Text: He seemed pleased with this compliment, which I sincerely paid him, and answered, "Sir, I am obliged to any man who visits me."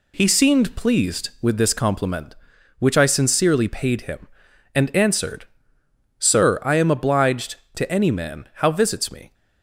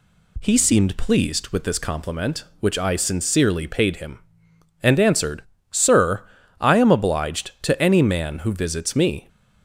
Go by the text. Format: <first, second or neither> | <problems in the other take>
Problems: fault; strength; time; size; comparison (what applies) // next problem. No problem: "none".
second | says "how" for "who"; at 8.5 s